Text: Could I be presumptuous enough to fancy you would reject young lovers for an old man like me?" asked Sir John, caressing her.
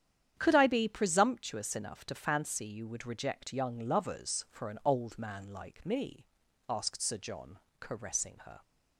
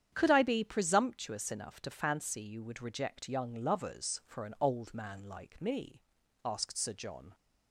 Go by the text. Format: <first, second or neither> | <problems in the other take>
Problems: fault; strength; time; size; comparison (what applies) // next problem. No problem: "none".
first | starts louder than the rest; strong; until 1.1 s; 9 dB; strong in the first // stops before "caressing her"; at 7.3 s